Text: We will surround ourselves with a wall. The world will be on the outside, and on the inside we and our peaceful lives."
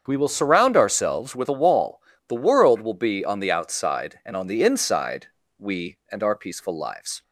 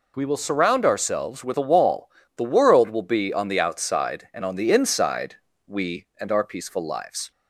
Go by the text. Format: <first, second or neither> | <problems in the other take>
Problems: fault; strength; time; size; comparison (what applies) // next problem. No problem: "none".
second | starts louder than the rest; strong; until 1.5 s; 7.5 dB // pauses between "inside" and "we"; slight; at 5.2 s; 0.32 s long; slight in the second